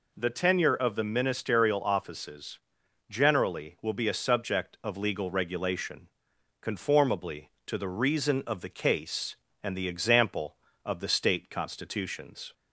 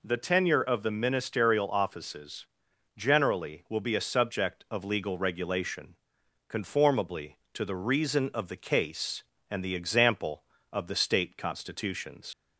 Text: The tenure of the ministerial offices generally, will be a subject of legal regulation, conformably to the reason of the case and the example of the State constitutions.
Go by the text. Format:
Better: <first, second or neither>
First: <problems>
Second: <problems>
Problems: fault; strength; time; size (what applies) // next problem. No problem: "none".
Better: first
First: pauses between "offices" and "generally"; noticeable; at 2.5 s; 0.50 s long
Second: pauses between "offices" and "generally"; noticeable; at 2.4 s; 0.50 s long // leaves "constitutions" unfinished; at 12.3 s; 70 ms